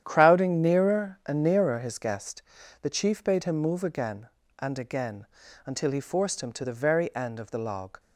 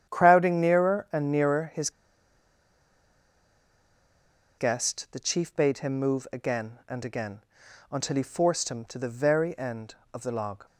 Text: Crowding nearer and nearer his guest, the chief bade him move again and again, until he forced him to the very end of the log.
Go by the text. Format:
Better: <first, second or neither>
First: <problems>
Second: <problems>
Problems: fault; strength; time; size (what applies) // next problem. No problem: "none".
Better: first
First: starts louder than the rest; strong; until 1.0 s; 10 dB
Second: starts louder than the rest; strong; until 1.1 s; 9.5 dB // pauses between "his" and "guest"; strong; at 1.8 s; 2.6 s long